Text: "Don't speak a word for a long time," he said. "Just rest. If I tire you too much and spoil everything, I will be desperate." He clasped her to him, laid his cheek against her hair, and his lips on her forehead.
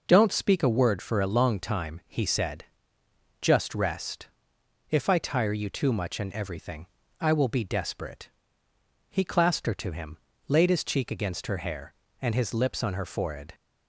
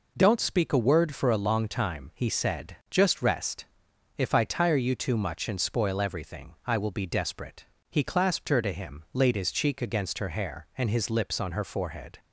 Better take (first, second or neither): second